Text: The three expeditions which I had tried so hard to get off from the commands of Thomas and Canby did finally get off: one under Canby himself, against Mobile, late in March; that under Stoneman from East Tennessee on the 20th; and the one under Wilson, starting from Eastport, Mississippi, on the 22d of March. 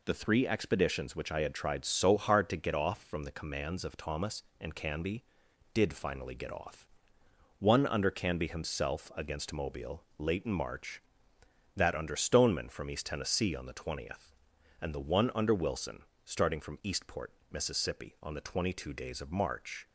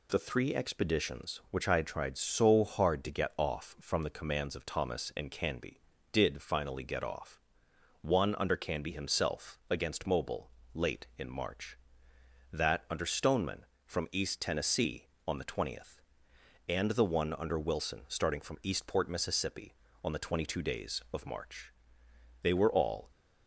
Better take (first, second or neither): first